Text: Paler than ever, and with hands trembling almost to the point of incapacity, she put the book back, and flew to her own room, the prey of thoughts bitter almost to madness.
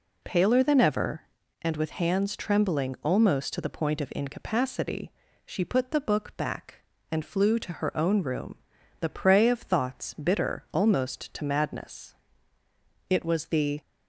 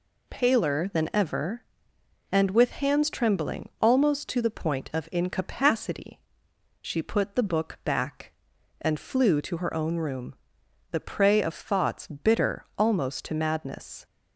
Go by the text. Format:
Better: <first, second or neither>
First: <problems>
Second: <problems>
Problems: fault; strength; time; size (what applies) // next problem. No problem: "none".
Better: second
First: goes on to say "It was the"; noticeable; from 13.0 s on; 0.72 s long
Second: none